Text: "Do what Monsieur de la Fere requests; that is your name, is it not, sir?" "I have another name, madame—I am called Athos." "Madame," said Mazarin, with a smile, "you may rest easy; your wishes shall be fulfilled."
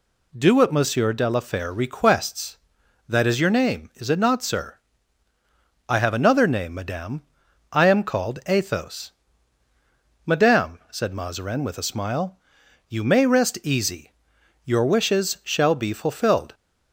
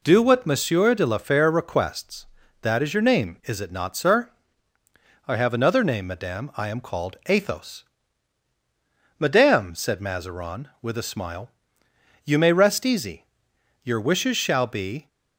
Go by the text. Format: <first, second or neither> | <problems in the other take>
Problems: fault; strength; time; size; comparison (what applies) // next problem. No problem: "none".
first | stops before "fulfilled"; at 15.0 s